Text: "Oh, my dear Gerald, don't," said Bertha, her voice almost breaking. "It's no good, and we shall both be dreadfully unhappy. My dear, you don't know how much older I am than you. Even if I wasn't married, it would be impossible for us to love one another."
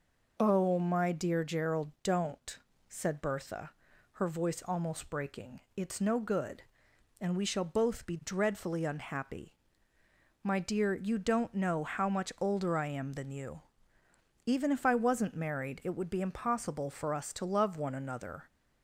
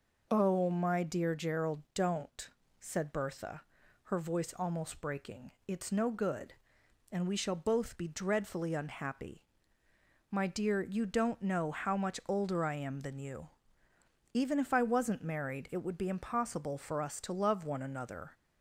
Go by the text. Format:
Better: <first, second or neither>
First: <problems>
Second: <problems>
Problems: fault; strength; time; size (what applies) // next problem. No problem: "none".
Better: neither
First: none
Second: none